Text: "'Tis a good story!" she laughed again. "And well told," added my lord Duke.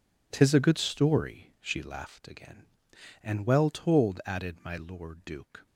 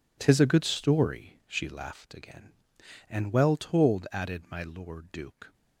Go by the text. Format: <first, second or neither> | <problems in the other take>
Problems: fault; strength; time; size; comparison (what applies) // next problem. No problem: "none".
neither | none